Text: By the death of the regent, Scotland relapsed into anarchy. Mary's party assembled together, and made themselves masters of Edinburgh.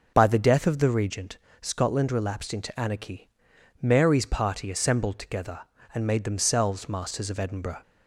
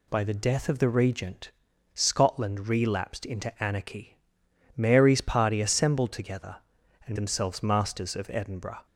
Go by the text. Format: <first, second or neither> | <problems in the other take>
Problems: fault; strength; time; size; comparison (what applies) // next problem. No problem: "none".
first | skips "made"; at 7.1 s